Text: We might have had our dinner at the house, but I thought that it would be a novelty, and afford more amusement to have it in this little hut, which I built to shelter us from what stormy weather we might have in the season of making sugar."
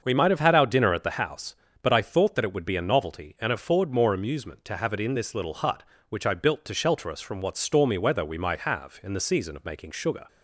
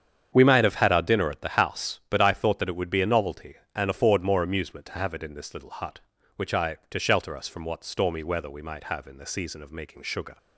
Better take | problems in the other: first | starts louder than the rest; strong; until 1.3 s; 8 dB; also in the first // skips "built"; at 6.8 s

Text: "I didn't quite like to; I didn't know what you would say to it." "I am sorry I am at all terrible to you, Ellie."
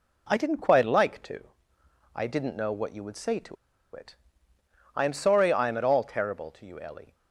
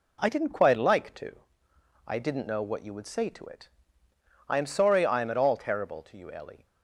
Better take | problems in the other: second | pauses between "to" and "it"; at 3.5 s; 0.37 s long

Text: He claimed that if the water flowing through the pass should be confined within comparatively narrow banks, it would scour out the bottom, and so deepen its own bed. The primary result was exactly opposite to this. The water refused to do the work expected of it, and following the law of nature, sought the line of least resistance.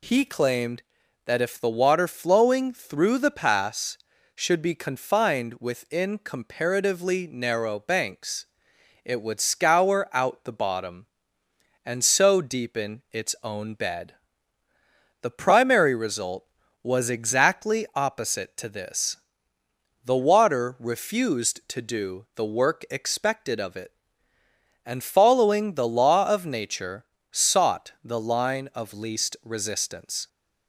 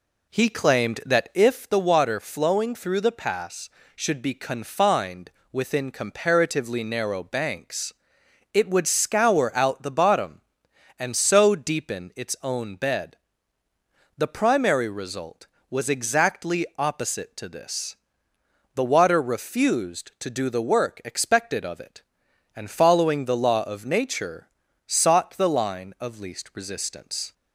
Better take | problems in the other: first | starts louder than the rest; slight; until 1.5 s; 2.5 dB // pauses between "confined" and "within"; slight; at 5.3 s; 0.20 s long

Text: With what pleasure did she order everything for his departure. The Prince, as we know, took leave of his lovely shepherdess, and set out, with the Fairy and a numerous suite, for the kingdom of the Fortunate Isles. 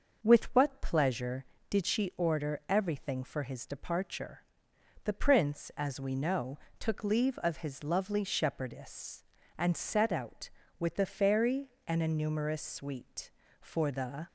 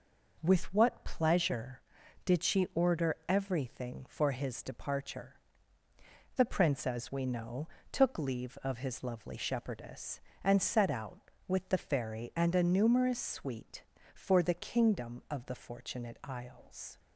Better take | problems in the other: second | starts louder than the rest; until 1.2 s; 6 dB // stops before "kingdom of the Fortunate Isles"; at 14.2 s

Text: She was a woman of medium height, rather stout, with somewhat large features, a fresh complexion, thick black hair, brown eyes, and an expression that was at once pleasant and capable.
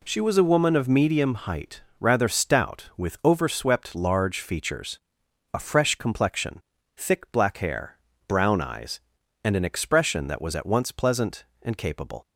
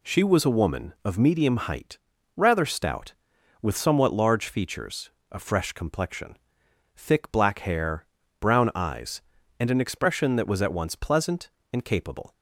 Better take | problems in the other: second | says "overswept" for "somewhat"; at 3.2 s

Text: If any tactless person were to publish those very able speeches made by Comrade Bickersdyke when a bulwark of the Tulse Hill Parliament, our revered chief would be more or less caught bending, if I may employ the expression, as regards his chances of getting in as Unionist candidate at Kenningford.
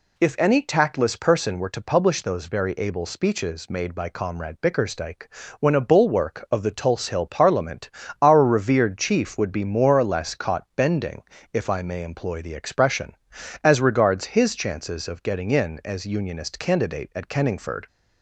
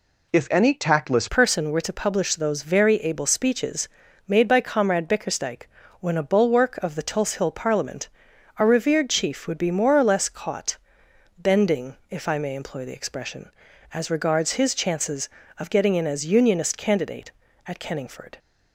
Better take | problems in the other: first | changes voice at "person"; from 1.2 s on; 17.1 s long // pauses between "speeches" and "made"; at 3.8 s; 0.40 s long // pauses between "Bickersdyke" and "when"; slight; at 5.6 s; 0.34 s long; slight in the first // pauses between "caught" and "bending"; noticeable; at 10.7 s; 0.60 s long

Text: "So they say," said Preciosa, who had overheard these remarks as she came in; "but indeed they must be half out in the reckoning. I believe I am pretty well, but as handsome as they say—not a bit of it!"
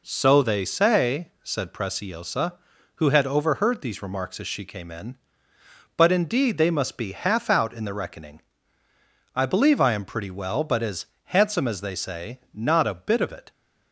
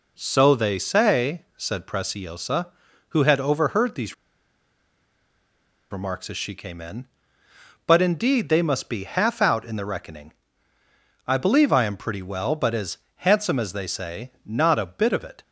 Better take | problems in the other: first | pauses between "these" and "remarks"; strong; at 4.1 s; 1.7 s long // pauses between "as" and "handsome"; slight; at 12.9 s; 0.20 s long; slight in the first

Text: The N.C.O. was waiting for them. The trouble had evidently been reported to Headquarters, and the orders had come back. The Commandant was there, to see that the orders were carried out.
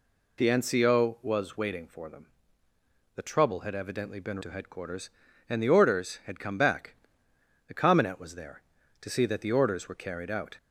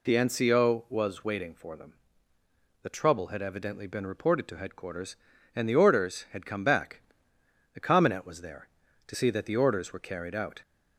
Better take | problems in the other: second | skips "reported"; at 4.3 s

